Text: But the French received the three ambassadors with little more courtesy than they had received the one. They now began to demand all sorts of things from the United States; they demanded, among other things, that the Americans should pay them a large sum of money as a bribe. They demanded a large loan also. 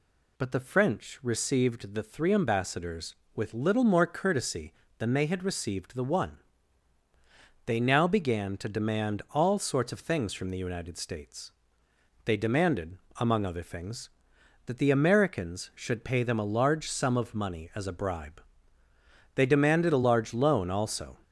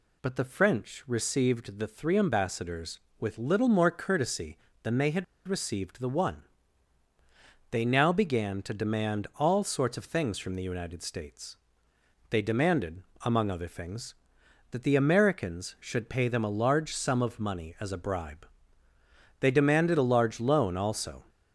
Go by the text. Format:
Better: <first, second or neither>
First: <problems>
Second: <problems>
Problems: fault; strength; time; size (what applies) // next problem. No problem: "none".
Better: first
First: none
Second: pauses between "had" and "received"; slight; at 5.2 s; 0.22 s long